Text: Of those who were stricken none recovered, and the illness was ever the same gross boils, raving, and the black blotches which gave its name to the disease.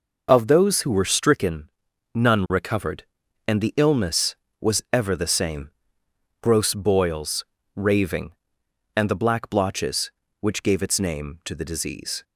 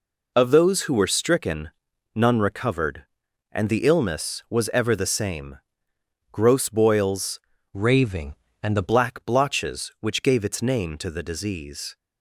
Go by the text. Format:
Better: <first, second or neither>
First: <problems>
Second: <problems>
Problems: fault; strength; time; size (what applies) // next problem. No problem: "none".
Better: first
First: pauses between "stricken" and "none"; at 1.6 s; 0.44 s long // pauses between "same" and "gross"; noticeable; at 5.6 s; 0.72 s long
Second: pauses between "stricken" and "none"; at 1.7 s; 0.44 s long // pauses between "same" and "gross"; noticeable; at 5.5 s; 0.74 s long // changes voice from "raving" to "the"; from 7.7 to 8.8 s; 1.1 s long